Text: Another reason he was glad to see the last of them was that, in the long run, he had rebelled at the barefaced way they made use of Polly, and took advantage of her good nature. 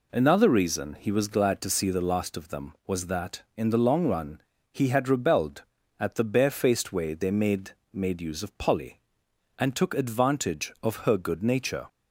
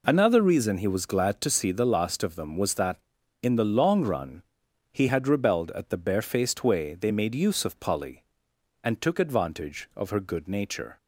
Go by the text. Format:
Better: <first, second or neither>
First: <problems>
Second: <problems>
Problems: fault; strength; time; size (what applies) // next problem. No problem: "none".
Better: second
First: says "made" twice; at 7.9 s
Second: none